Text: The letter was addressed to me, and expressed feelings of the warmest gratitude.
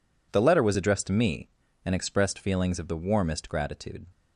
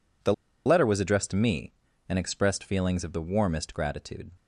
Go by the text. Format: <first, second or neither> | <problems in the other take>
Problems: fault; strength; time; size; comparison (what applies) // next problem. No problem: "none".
first | pauses between "The" and "letter"; slight; at 0.3 s; 0.31 s long